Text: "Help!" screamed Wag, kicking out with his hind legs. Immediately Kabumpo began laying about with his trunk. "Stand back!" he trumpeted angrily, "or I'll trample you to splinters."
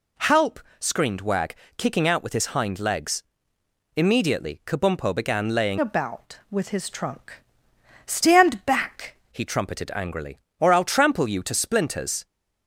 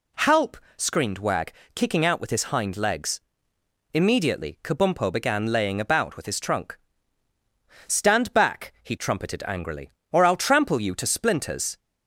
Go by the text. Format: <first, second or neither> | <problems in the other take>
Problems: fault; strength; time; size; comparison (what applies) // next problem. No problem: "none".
second | changes voice from "about" to "back"; from 5.7 to 9.1 s; 3.4 s long